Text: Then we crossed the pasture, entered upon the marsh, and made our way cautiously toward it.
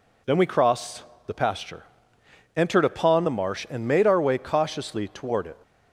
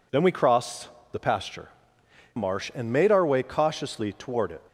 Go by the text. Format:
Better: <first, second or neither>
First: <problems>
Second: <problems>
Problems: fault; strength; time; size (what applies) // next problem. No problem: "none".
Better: first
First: pauses between "crossed" and "the"; slight; at 1.0 s; 0.24 s long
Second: pauses between "crossed" and "the"; slight; at 0.8 s; 0.24 s long // skips "entered upon the"; at 2.0 s